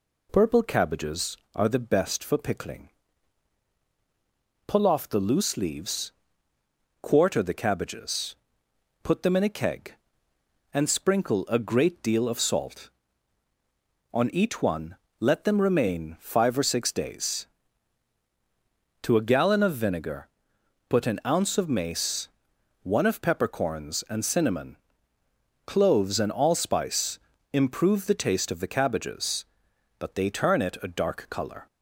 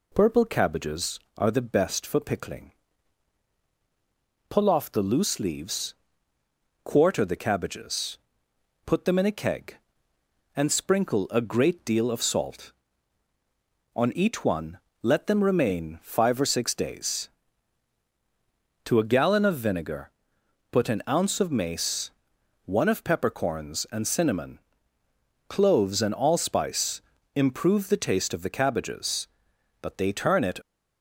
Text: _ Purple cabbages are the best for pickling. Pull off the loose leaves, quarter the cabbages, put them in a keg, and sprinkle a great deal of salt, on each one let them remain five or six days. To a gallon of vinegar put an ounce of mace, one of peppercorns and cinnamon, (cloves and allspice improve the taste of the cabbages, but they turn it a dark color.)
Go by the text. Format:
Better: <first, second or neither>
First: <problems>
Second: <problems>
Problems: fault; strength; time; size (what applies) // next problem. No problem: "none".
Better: first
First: pauses between "one" and "let"; slight; at 14.9 s; 0.24 s long // pauses between "vinegar" and "put"; noticeable; at 20.2 s; 0.60 s long // pauses between "allspice" and "improve"; slight; at 27.1 s; 0.34 s long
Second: pauses between "one" and "let"; slight; at 14.7 s; 0.24 s long // pauses between "vinegar" and "put"; noticeable; at 20.1 s; 0.60 s long // pauses between "allspice" and "improve"; slight; at 27.0 s; 0.34 s long // stops before "a dark color"; at 30.6 s